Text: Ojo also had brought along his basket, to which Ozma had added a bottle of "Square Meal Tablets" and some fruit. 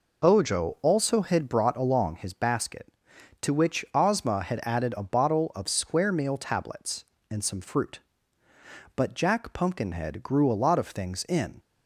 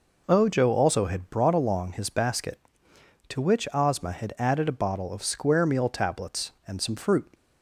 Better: second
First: goes on to say "But Jack Pumpkinhead grew a lot of things in"; strong; from 8.9 s on; 2.6 s long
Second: none

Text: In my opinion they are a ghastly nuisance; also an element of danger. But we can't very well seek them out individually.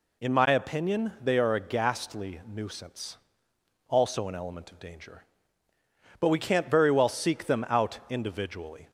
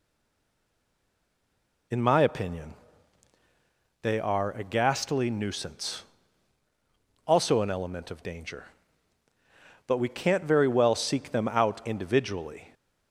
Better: first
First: none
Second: stays silent before the first word; noticeable; until 1.9 s; 1.9 s long // pauses between "opinion" and "they"; strong; at 2.7 s; 1.2 s long

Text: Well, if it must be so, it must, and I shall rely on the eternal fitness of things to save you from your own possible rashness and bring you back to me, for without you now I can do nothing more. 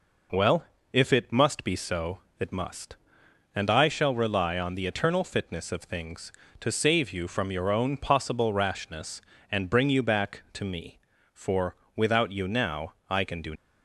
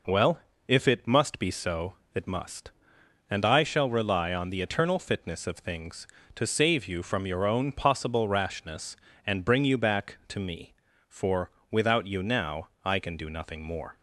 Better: second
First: pauses between "for" and "without"; slight; at 11.7 s; 0.22 s long // pauses between "now" and "I"; slight; at 12.9 s; 0.16 s long // stops before "nothing more"; at 13.5 s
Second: pauses between "for" and "without"; slight; at 11.4 s; 0.22 s long // pauses between "now" and "I"; slight; at 12.6 s; 0.16 s long

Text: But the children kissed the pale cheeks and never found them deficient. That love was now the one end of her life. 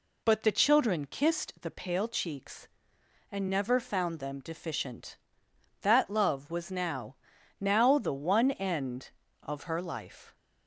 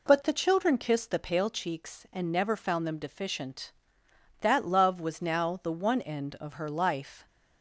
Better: second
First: says "now" twice; at 7.5 s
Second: none

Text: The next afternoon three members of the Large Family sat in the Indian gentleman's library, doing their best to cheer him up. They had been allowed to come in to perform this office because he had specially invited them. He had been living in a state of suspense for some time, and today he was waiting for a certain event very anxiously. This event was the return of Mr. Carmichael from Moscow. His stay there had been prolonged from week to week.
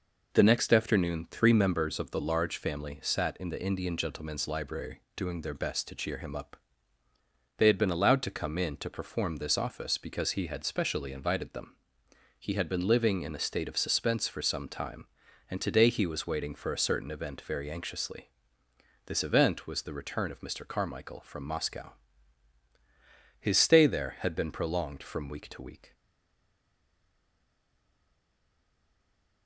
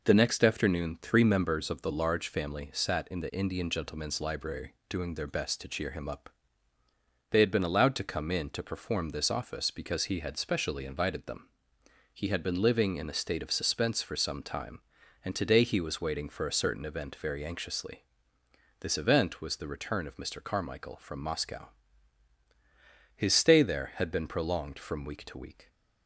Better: second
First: stays silent after the last word; strong; from 25.9 s on; 3.5 s long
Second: none

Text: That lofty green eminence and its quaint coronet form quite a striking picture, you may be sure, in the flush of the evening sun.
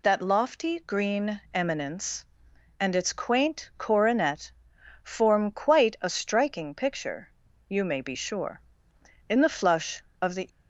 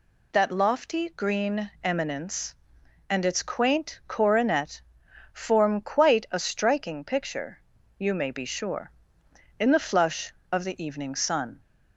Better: second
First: pauses between "coronet" and "form"; noticeable; at 4.5 s; 0.50 s long // stops before "evening sun"; at 10.4 s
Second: pauses between "coronet" and "form"; noticeable; at 4.8 s; 0.50 s long

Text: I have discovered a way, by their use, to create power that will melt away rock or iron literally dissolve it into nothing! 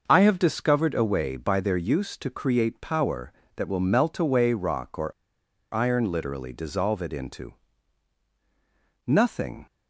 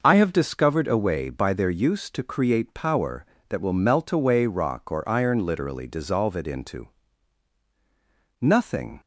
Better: second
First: starts louder than the rest; noticeable; until 1.0 s; 6 dB // pauses between "or" and "iron"; noticeable; at 5.1 s; 0.61 s long // pauses between "into" and "nothing"; strong; at 7.5 s; 1.5 s long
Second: pauses between "into" and "nothing"; strong; at 6.8 s; 1.5 s long

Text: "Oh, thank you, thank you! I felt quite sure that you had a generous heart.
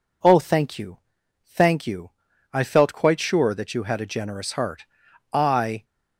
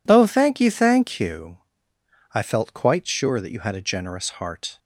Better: second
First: goes on to say "I"; from 5.3 s on; 0.52 s long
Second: none

